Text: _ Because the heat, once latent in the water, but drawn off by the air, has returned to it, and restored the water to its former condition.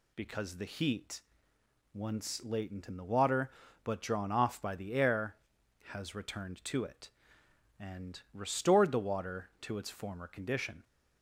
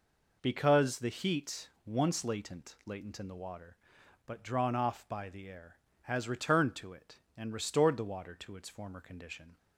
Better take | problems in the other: first | says "latent" twice; at 2.8 s

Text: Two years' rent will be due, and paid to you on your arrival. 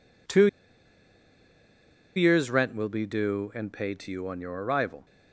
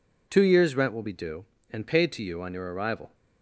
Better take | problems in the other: second | pauses between "Two" and "years"; strong; at 0.4 s; 1.6 s long

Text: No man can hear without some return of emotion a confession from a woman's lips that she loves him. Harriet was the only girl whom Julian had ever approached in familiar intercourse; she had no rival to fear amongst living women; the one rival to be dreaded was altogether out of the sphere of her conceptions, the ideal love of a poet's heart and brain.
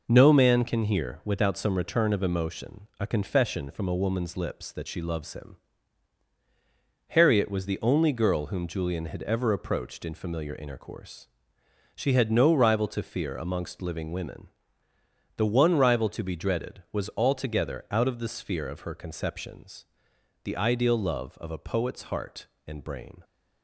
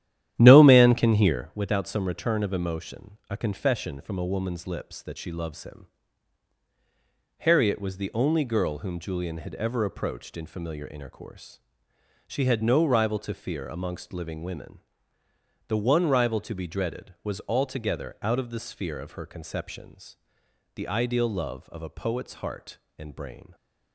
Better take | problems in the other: first | starts louder than the rest; strong; until 1.5 s; 11.5 dB

